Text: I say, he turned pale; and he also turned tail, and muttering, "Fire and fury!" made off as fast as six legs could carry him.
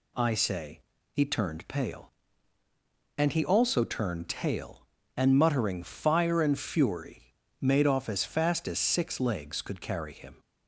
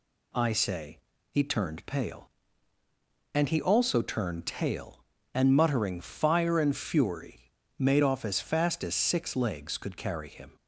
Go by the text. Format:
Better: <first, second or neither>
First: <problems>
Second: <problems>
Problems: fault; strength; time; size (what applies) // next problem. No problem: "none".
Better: neither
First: none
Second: none